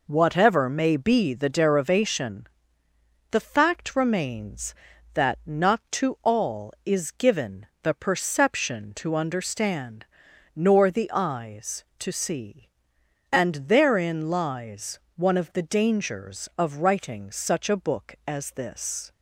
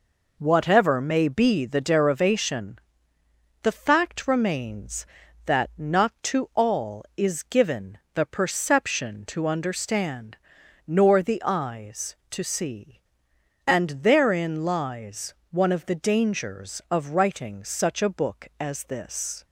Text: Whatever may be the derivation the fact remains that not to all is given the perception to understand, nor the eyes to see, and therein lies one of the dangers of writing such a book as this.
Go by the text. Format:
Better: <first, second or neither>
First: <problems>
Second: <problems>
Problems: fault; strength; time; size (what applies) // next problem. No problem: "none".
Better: neither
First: pauses between "derivation" and "the"; noticeable; at 2.4 s; 0.86 s long // pauses between "given" and "the"; slight; at 7.6 s; 0.16 s long // pauses between "lies" and "one"; slight; at 14.9 s; 0.16 s long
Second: pauses between "derivation" and "the"; noticeable; at 2.7 s; 0.86 s long // pauses between "given" and "the"; slight; at 7.9 s; 0.16 s long // pauses between "lies" and "one"; slight; at 15.3 s; 0.16 s long